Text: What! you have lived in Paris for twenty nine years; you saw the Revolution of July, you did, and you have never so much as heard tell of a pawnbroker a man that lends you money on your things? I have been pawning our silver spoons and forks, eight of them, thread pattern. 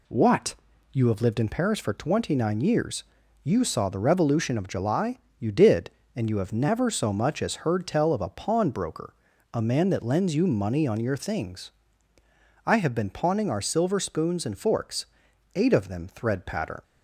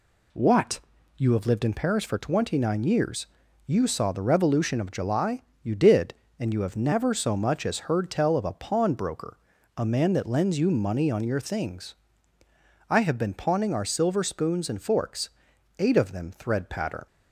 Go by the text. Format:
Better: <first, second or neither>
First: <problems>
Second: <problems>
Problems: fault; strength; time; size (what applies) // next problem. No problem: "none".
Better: neither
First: pauses between "pawnbroker" and "a"; at 9.1 s; 0.40 s long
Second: pauses between "pawnbroker" and "a"; at 9.3 s; 0.40 s long